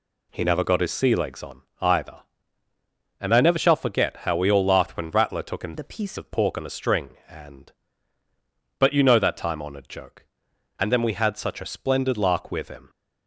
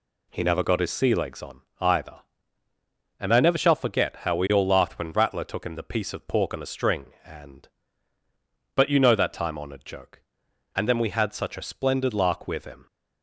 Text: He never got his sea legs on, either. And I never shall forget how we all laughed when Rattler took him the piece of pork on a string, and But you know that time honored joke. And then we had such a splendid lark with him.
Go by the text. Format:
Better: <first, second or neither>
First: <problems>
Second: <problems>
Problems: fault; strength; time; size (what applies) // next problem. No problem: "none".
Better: second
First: changes voice from "the" to "piece"; from 5.7 to 6.1 s; 0.4 s long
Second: none